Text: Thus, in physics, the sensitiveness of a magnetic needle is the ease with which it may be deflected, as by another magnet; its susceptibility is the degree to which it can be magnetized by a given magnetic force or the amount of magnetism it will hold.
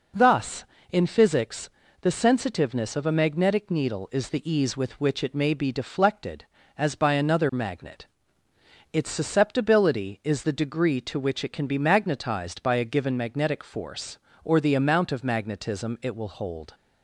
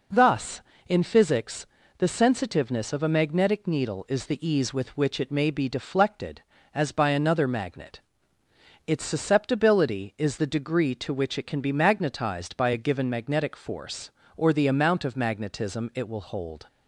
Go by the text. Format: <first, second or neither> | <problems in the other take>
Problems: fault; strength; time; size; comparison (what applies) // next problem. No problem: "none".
neither | none